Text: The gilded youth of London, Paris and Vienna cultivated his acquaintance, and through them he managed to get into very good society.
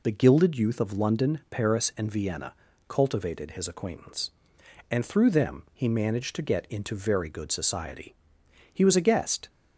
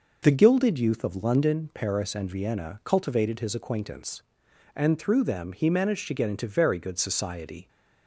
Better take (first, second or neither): second